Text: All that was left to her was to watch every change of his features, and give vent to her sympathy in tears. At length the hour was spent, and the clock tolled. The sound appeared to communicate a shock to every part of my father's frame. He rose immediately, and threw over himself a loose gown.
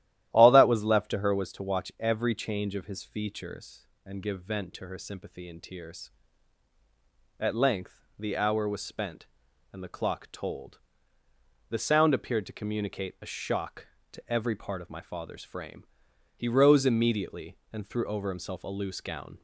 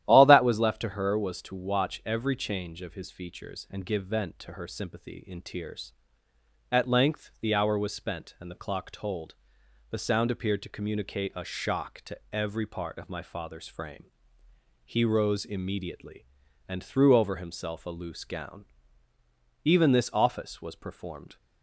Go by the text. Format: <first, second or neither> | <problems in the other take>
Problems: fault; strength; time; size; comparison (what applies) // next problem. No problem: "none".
first | starts louder than the rest; strong; until 1.0 s; 12 dB; strong in the first // goes on to say "Even this office was performed"; strong; from 19.6 s on; 1.7 s long